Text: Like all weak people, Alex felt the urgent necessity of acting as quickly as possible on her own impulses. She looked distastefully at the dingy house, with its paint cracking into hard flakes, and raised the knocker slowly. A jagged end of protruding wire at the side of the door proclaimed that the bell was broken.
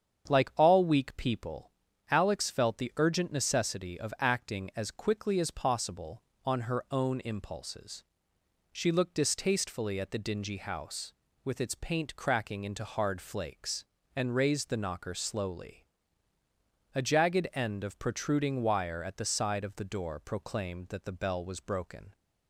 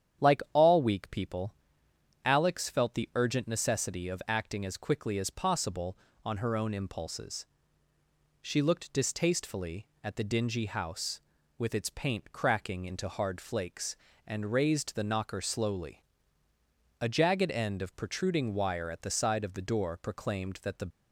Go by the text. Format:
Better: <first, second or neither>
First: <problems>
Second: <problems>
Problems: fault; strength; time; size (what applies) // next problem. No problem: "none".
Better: first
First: starts louder than the rest; strong; until 1.3 s; 8 dB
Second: starts louder than the rest; strong; until 1.3 s; 9 dB // stops before "bell was broken"; at 20.9 s